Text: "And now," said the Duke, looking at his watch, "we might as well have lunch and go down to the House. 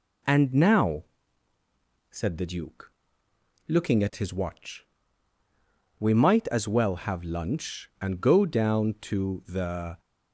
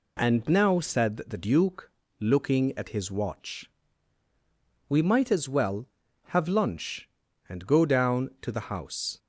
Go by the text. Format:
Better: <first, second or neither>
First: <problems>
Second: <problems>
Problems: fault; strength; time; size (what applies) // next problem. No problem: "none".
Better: second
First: stops before "House"; at 9.9 s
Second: none